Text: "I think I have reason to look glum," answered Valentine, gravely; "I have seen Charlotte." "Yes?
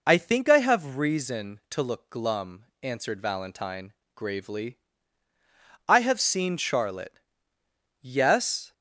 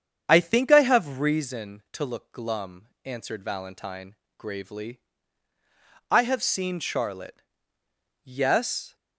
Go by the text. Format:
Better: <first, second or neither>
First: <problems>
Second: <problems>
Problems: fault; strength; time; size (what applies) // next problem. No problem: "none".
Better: first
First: none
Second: starts louder than the rest; strong; until 1.5 s; 8 dB